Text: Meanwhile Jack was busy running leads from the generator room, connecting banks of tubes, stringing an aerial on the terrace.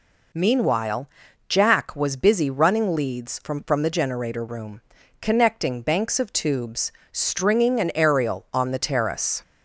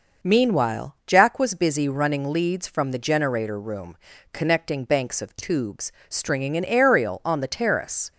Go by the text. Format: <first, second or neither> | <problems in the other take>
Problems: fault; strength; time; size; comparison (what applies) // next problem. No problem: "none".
second | pauses between "Meanwhile" and "Jack"; at 1.0 s; 0.40 s long // says "from" twice; at 3.6 s